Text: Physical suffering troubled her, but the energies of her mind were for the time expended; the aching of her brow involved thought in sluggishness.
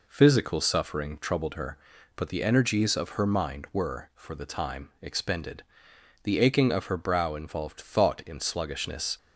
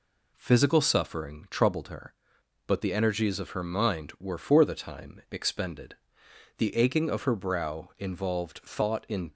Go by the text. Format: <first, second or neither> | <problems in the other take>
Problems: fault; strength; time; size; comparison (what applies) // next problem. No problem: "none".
first | stops before "sluggishness"; at 9.3 s